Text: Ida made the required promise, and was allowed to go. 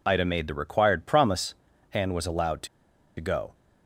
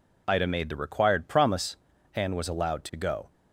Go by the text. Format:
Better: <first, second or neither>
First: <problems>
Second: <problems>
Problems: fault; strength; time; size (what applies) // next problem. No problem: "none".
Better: second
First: pauses between "to" and "go"; noticeable; at 2.6 s; 0.51 s long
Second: none